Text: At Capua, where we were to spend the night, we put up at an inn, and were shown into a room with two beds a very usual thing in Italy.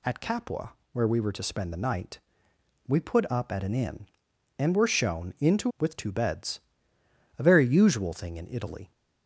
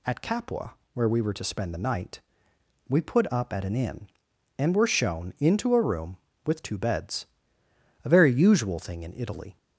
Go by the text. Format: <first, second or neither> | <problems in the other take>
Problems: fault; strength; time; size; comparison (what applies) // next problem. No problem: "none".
second | skips "a room"; at 5.7 s // pauses between "beds" and "a"; noticeable; at 6.5 s; 0.80 s long; noticeable in the second